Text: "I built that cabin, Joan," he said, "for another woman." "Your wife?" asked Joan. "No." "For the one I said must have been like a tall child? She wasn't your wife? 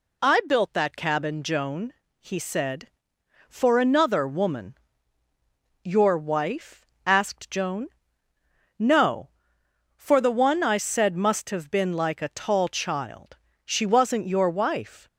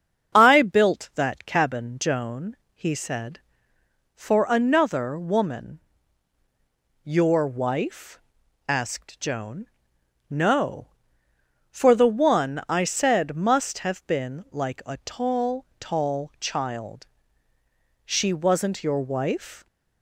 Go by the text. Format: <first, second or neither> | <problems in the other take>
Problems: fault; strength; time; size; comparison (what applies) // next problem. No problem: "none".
first | starts louder than the rest; until 1.3 s; 7 dB // says "tall" twice; at 15.7 s